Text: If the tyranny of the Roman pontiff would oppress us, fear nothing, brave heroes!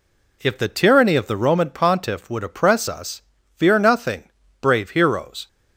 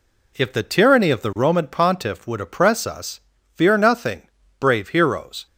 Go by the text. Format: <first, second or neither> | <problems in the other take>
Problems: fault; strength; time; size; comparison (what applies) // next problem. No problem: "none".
neither | none